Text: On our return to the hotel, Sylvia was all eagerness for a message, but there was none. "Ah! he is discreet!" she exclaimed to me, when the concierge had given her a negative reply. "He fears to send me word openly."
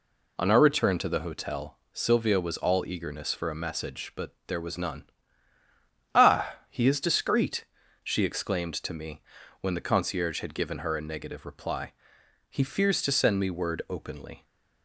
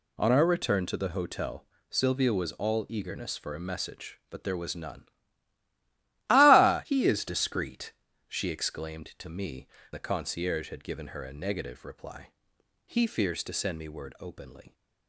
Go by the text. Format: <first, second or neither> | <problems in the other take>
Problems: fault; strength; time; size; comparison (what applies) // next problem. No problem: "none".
first | skips "when"; at 9.7 s